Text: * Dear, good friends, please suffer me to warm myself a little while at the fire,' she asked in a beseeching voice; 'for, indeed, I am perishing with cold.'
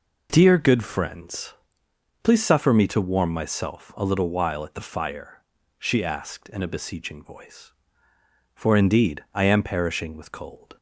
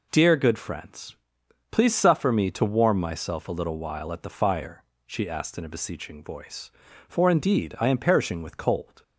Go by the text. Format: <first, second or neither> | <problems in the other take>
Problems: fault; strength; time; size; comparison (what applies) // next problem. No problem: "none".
neither | none